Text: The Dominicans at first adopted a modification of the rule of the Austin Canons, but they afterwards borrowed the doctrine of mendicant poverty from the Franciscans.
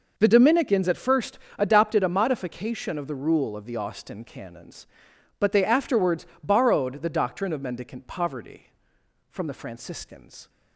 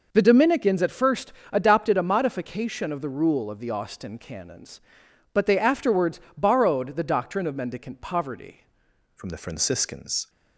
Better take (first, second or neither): first